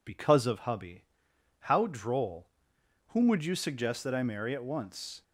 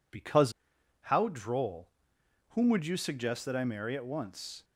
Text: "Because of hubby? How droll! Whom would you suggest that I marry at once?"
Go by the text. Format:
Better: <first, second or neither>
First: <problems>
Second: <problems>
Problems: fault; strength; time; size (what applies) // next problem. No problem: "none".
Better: first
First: none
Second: skips "of hubby"; at 0.7 s